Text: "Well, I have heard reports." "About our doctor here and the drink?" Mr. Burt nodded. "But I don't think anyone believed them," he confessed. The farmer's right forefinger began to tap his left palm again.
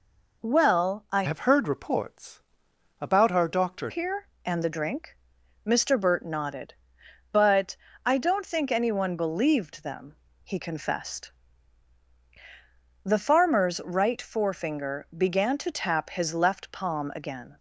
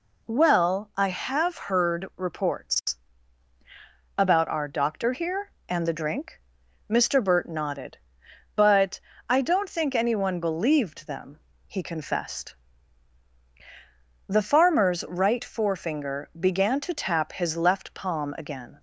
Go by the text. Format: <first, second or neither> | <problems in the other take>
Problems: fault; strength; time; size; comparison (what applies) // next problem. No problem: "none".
second | changes voice from "have" to "doctor"; from 1.2 to 3.9 s; 2.7 s long // pauses between "But" and "I"; slight; at 7.7 s; 0.28 s long; slight in the second